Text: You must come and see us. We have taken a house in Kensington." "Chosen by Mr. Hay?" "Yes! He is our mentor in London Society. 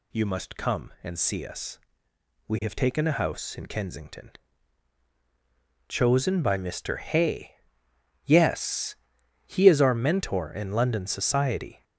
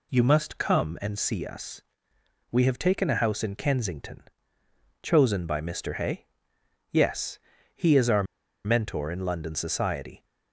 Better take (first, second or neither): first